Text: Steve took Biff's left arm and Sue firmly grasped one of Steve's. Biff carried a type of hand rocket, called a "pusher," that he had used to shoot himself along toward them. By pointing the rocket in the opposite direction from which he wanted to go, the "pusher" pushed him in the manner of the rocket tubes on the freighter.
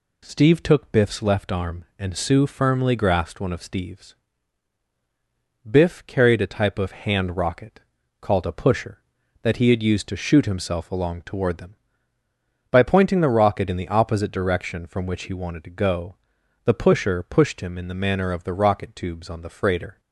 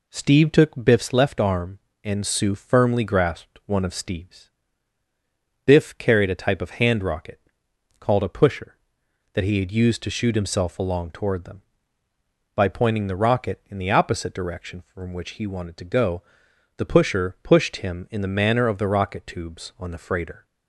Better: neither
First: none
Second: none

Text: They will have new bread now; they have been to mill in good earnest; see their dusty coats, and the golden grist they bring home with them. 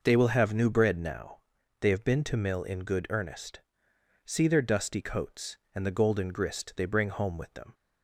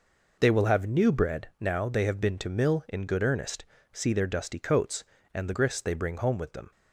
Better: first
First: none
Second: skips "golden"; at 5.5 s

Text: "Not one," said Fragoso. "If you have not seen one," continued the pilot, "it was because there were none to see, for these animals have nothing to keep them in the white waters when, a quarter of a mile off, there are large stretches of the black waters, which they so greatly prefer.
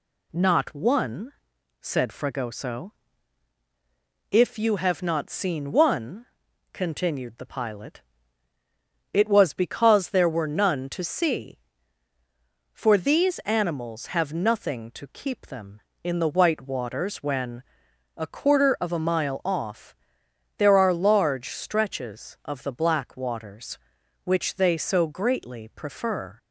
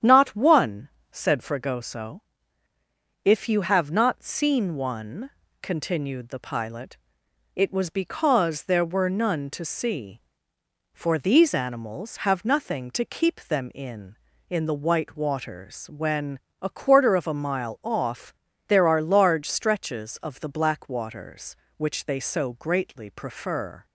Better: first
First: none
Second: starts louder than the rest; strong; until 1.2 s; 9 dB // says "in" twice; at 14.4 s

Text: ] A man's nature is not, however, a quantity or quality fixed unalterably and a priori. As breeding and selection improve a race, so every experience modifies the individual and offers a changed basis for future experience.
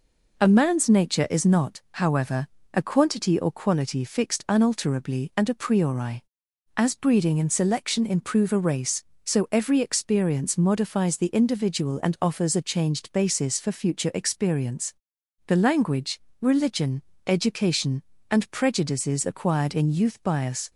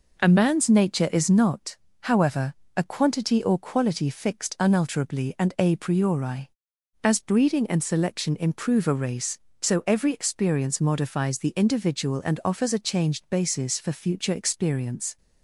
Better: second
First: goes on to say "The language religion education and prejudices acquired in youth bias"; strong; from 15.4 s on; 5.2 s long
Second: none

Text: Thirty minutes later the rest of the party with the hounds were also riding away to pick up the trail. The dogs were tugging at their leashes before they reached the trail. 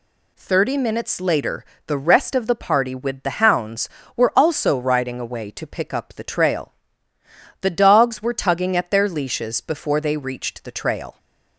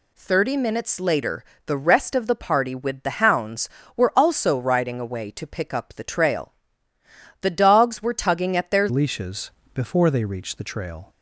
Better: first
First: pauses between "later" and "the"; slight; at 1.6 s; 0.22 s long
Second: pauses between "later" and "the"; slight; at 1.4 s; 0.22 s long // changes voice at "leashes"; from 8.9 s on; 2.2 s long // pauses between "leashes" and "before"; slight; at 9.5 s; 0.22 s long

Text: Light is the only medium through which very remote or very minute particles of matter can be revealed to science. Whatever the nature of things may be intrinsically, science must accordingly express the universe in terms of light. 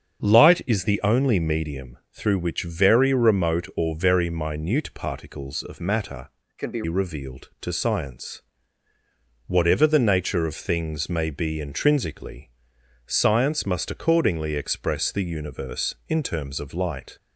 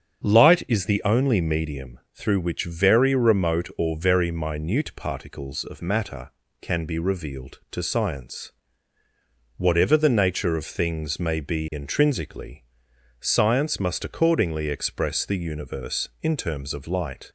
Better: second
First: starts louder than the rest; strong; until 1.3 s; 7 dB // pauses between "medium" and "through"; slight; at 1.9 s; 0.16 s long // changes voice from "can" to "be"; from 6.5 to 6.8 s; 0.3 s long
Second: starts louder than the rest; strong; until 1.3 s; 7.5 dB // pauses between "medium" and "through"; slight; at 1.9 s; 0.16 s long

